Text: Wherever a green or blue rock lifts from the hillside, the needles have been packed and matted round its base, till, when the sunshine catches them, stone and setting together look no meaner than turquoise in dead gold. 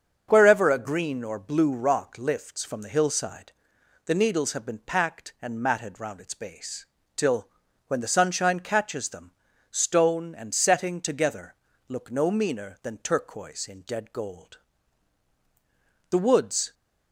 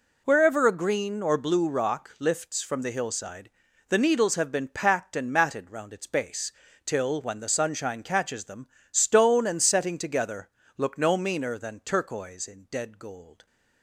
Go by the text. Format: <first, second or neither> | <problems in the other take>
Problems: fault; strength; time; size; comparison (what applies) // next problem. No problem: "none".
second | starts louder than the rest; until 1.3 s; 6.5 dB // pauses between "together" and "look"; slight; at 11.5 s; 0.32 s long; slight in the second // goes on to say "The woods"; noticeable; from 16.1 s on; 0.62 s long